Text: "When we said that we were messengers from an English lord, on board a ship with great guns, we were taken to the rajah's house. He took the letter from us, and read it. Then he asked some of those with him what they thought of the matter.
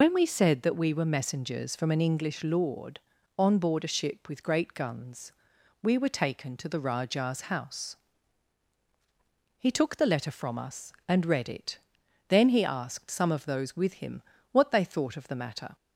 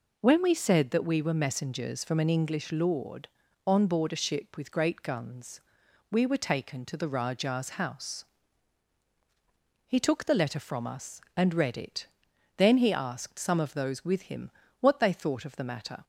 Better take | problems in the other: second | loses the start of "When"; at 0.0 s; 95 ms // pauses between "him" and "what"; slight; at 14.2 s; 0.30 s long; slight in the second

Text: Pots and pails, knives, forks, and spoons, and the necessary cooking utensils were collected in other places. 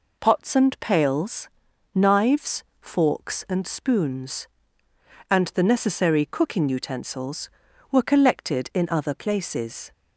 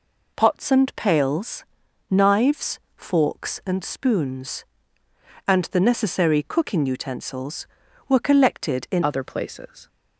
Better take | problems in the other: first | changes voice at "other"; from 9.0 s on; 0.8 s long

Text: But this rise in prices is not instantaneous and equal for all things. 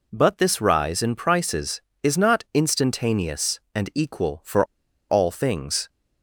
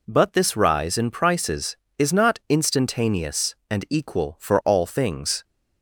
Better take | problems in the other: second | pauses between "for" and "all"; at 4.6 s; 0.45 s long

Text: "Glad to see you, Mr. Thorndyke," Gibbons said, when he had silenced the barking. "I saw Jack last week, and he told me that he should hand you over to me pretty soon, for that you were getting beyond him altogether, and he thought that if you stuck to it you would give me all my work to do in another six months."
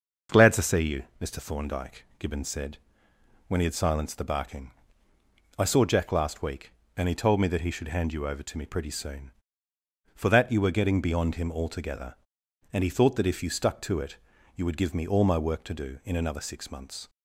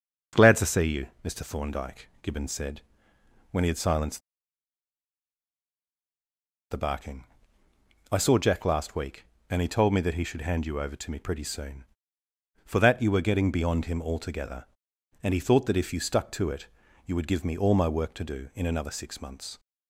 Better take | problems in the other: first | starts louder than the rest; noticeable; until 1.5 s; 6 dB; noticeable in the first // pauses between "silenced" and "the"; strong; at 4.1 s; 2.5 s long // pauses between "it" and "you"; at 16.6 s; 0.38 s long; also in the first

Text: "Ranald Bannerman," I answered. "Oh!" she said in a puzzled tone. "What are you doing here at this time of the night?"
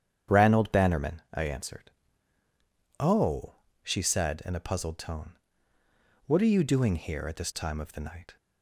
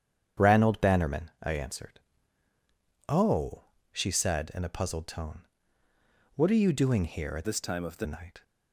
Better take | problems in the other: first | starts louder than the rest; strong; until 1.4 s; 9 dB; strong in the first // changes voice from "this" to "the"; from 7.4 to 8.0 s; 0.6 s long

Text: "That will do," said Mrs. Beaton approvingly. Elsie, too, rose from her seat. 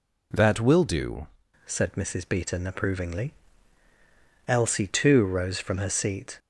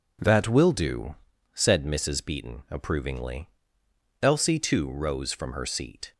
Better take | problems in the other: second | changes voice at "said"; from 1.6 s on; 4.7 s long

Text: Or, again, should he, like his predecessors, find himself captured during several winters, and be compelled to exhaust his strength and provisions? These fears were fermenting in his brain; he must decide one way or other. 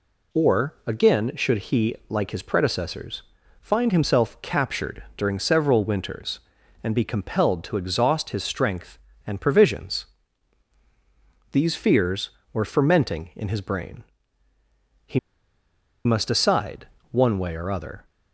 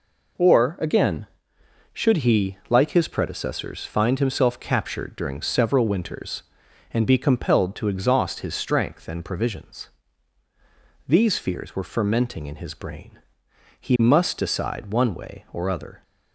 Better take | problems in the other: second | pauses between "he" and "must"; noticeable; at 15.1 s; 0.86 s long // pauses between "decide" and "one"; slight; at 16.8 s; 0.22 s long

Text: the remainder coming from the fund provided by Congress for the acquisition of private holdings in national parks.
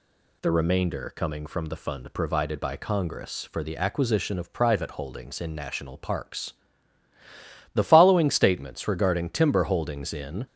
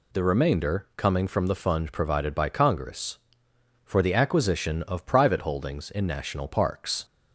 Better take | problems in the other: second | goes on to say "The following statements regarding timber holdings in"; strong; from 7.7 s on; 2.7 s long

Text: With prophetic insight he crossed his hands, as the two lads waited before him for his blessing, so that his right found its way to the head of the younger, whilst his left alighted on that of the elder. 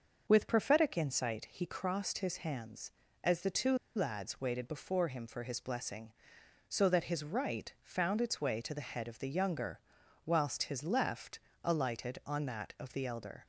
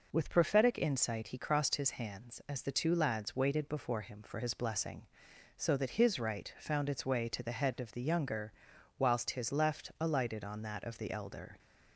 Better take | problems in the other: second | pauses between "two" and "lads"; slight; at 3.7 s; 0.18 s long // pauses between "left" and "alighted"; slight; at 11.3 s; 0.24 s long

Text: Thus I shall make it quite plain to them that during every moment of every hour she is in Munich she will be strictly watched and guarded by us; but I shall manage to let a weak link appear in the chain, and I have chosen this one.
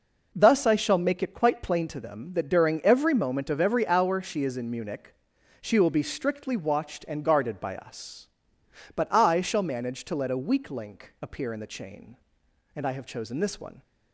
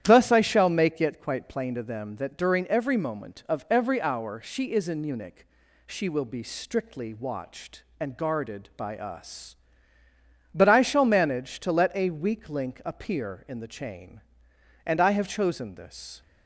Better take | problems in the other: first | starts louder than the rest; strong; until 1.0 s; 11 dB // pauses between "Munich" and "she"; at 5.4 s; 0.40 s long; noticeable in the first // stops before "one"; at 16.2 s

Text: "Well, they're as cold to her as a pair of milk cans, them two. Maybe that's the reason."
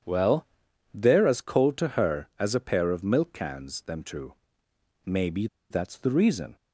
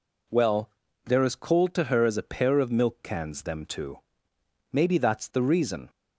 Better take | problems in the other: second | starts louder than the rest; strong; until 1.4 s; 8.5 dB // pauses between "Maybe" and "that's"; slight; at 5.4 s; 0.24 s long

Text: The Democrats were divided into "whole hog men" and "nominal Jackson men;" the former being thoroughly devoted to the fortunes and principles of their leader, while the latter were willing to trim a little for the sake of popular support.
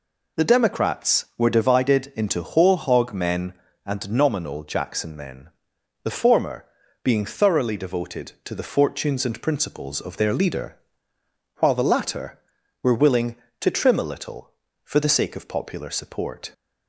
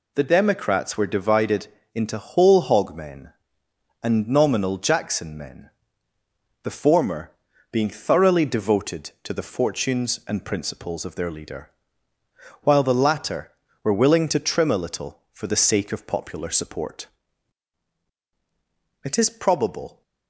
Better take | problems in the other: first | pauses between "divided" and "into"; slight; at 1.6 s; 0.26 s long // pauses between "former" and "being"; at 7.2 s; 0.40 s long; slight in the first // goes on to say "It is probable"; noticeable; from 19.0 s on; 0.98 s long

